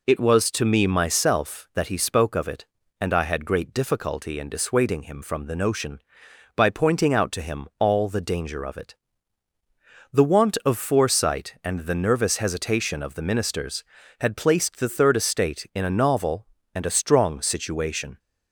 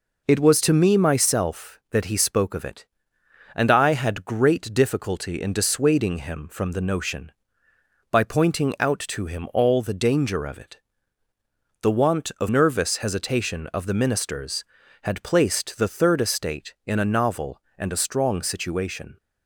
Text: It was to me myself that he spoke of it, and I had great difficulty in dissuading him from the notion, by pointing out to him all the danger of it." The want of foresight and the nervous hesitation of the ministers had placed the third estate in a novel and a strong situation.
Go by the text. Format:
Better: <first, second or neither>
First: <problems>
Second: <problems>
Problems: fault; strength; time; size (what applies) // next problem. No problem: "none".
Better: first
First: none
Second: skips "foresight and the"; at 12.4 s